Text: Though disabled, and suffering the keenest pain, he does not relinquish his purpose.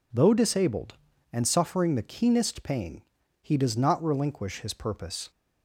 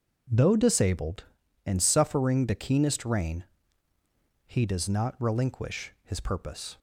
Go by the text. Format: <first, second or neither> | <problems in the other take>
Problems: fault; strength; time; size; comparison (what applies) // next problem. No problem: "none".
first | says "rain" for "pain"; at 3.0 s